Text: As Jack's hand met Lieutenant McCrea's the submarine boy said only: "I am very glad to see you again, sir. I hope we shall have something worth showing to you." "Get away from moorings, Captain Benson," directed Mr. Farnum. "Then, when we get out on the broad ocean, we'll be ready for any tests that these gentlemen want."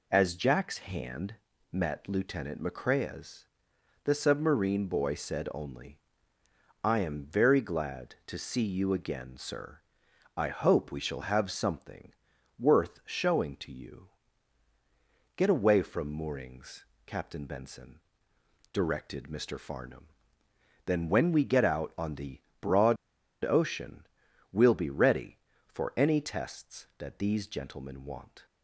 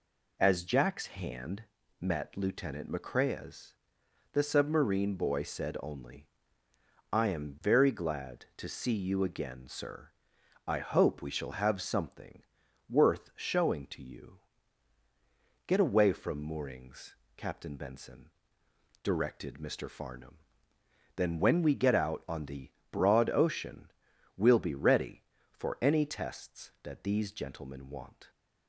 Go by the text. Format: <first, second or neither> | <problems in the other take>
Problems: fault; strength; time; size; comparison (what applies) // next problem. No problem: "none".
second | pauses between "hand" and "met"; slight; at 1.3 s; 0.36 s long; slight in the second // pauses between "McCrea's" and "the"; noticeable; at 3.4 s; 0.60 s long; noticeable in the second // pauses between "something" and "worth"; noticeable; at 12.1 s; 0.46 s long; noticeable in the second // pauses between "the" and "broad"; slight; at 22.4 s; 0.20 s long; slight in the second // pauses between "broad" and "ocean"; noticeable; at 22.9 s; 0.47 s long